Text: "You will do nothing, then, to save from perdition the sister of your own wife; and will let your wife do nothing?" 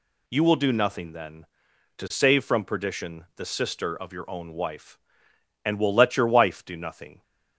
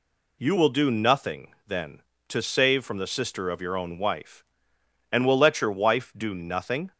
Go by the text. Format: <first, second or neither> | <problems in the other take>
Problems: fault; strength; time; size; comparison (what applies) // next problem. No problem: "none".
first | skips "perdition"; at 2.9 s